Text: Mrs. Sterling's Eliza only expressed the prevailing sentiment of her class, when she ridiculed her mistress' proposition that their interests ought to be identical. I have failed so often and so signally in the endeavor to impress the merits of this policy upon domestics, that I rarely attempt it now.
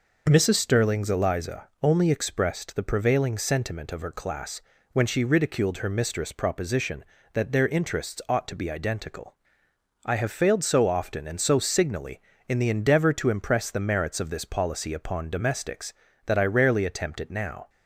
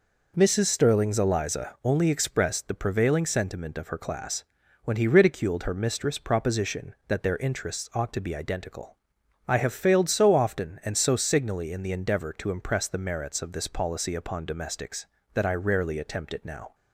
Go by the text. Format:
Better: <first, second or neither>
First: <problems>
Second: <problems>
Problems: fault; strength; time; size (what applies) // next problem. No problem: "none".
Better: first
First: none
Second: says "he" for "she"; at 4.9 s